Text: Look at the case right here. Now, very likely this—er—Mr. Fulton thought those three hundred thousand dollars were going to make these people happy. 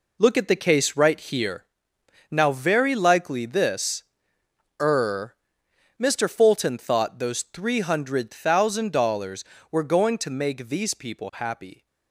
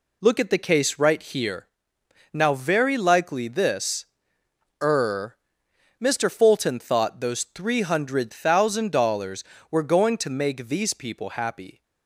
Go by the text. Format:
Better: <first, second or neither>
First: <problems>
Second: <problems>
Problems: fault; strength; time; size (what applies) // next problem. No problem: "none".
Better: second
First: gets quieter; strong; throughout; 9.5 dB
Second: none